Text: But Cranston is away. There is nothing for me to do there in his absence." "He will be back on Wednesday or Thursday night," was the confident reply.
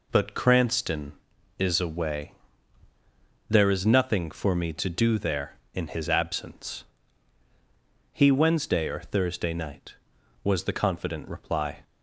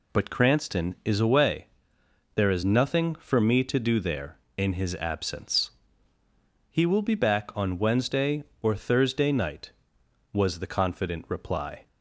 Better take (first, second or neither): second